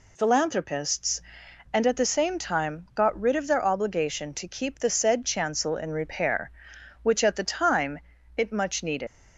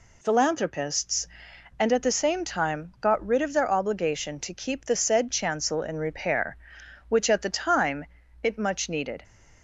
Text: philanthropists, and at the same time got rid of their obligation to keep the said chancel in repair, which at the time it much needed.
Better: second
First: pauses between "time" and "it"; at 7.9 s; 0.38 s long // leaves "needed" unfinished; at 9.0 s; 100 ms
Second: pauses between "time" and "it"; at 8.0 s; 0.38 s long

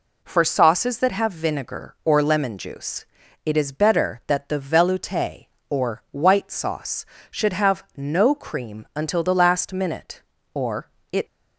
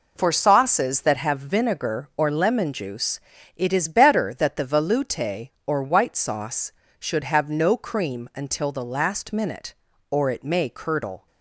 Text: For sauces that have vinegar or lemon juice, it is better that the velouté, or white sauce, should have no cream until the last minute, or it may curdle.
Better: second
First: pauses between "or" and "it"; slight; at 10.8 s; 0.22 s long // stops before "may curdle"; at 11.2 s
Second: none

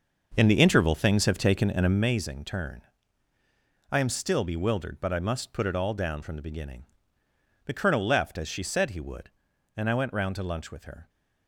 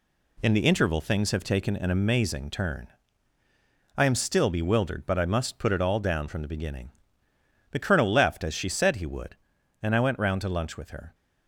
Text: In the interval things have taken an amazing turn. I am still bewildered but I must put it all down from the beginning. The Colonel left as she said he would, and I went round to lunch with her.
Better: second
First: starts louder than the rest; until 2.2 s; 6 dB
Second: none

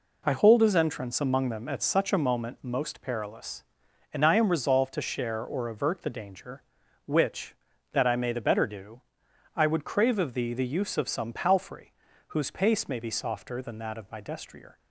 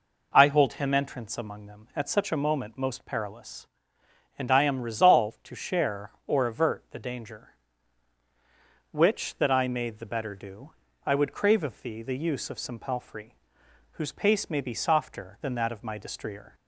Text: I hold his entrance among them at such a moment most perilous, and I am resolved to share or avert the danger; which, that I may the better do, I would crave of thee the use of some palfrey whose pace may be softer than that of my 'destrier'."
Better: first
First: pauses between "palfrey" and "whose"; slight; at 11.9 s; 0.36 s long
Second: says "him" for "his"; at 0.7 s // pauses between "palfrey" and "whose"; noticeable; at 13.3 s; 0.62 s long

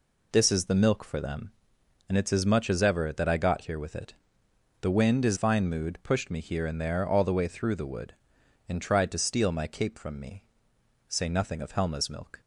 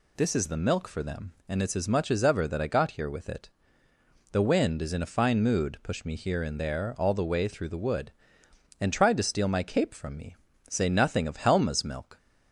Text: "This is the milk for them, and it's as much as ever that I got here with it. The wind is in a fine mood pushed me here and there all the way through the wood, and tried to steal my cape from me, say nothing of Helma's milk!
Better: second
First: skips "in a"; at 5.3 s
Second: none

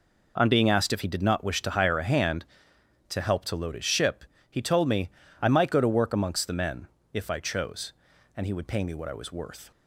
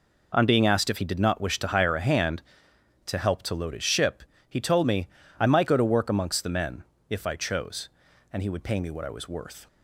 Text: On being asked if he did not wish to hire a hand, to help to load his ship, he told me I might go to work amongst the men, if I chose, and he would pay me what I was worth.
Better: neither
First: pauses between "me" and "I"; slight; at 5.0 s; 0.32 s long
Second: pauses between "me" and "I"; slight; at 5.0 s; 0.32 s long

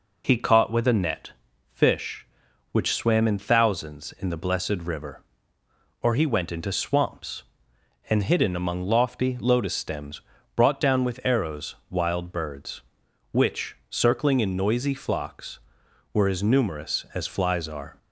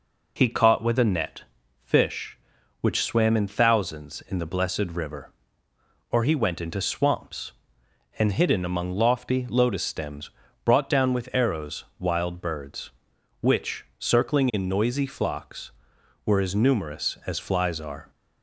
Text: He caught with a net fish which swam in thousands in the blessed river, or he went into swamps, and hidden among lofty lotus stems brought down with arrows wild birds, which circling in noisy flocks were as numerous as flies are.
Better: neither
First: pauses between "net" and "fish"; slight; at 1.3 s; 0.36 s long // pauses between "stems" and "brought"; slight; at 10.1 s; 0.34 s long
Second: pauses between "net" and "fish"; slight; at 1.4 s; 0.36 s long // pauses between "stems" and "brought"; slight; at 10.2 s; 0.34 s long

